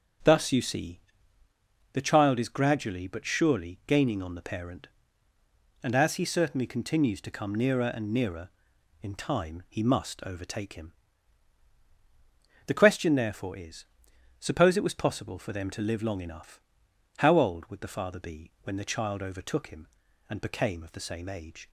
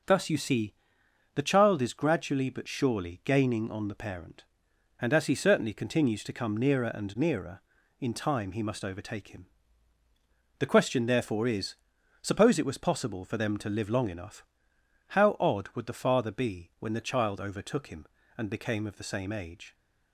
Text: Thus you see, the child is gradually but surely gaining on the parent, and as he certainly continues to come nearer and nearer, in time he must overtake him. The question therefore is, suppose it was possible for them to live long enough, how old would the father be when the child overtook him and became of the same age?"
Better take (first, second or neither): first